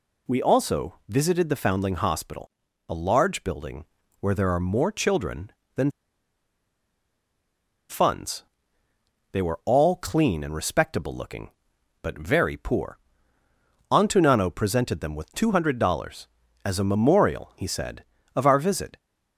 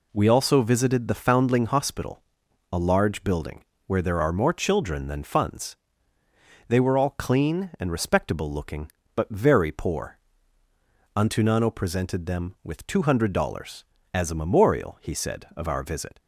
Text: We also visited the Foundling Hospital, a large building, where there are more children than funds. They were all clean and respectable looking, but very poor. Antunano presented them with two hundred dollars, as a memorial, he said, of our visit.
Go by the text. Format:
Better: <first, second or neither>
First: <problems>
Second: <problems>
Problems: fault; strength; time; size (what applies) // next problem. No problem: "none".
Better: second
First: pauses between "than" and "funds"; strong; at 5.8 s; 2.0 s long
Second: none